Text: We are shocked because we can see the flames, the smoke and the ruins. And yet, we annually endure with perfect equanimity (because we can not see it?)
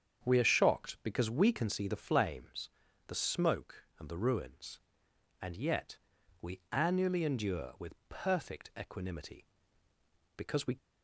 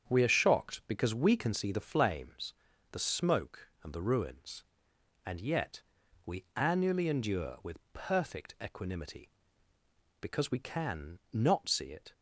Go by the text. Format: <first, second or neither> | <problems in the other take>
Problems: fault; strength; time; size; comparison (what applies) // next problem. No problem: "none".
second | starts louder than the rest; strong; until 1.2 s; 7.5 dB; strong in the second // stops before "can not see it"; at 10.7 s